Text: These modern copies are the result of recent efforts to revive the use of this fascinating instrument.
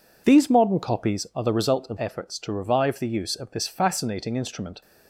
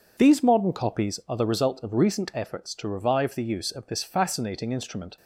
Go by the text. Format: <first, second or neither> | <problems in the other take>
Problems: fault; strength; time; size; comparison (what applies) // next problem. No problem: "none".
second | skips "recent"; at 1.9 s